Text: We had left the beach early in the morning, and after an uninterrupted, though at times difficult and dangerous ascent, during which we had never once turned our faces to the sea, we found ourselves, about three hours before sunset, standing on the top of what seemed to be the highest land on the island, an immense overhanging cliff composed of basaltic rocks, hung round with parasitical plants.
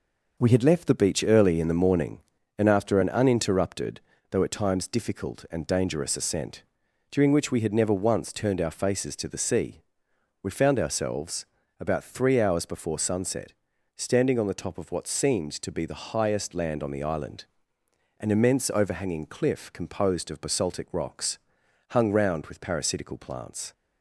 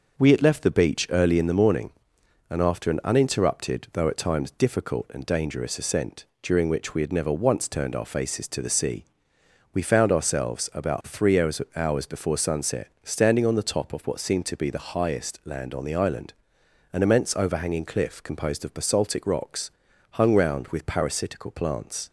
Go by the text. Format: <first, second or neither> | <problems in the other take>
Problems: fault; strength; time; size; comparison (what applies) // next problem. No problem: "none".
first | starts louder than the rest; noticeable; until 1.2 s; 6 dB // says "hours" twice; at 11.7 s